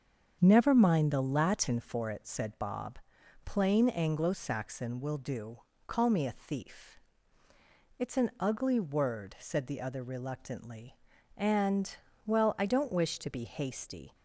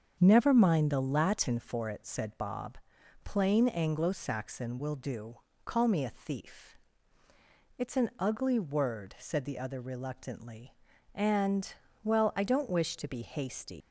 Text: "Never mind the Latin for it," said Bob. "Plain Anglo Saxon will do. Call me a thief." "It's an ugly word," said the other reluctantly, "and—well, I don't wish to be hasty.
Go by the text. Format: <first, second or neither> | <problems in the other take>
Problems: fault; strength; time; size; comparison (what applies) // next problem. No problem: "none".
first | starts louder than the rest; until 1.2 s; 7 dB; strong in the first // leaves "hasty" unfinished; at 13.8 s; 115 ms